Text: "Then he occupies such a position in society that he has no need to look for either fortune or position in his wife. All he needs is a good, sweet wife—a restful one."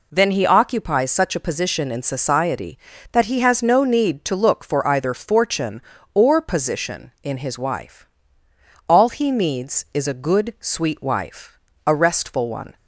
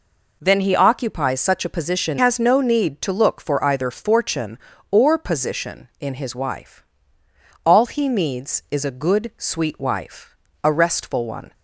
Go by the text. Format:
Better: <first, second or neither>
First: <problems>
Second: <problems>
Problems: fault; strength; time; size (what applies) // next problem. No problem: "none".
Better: first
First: none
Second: skips "in society that he"; at 2.1 s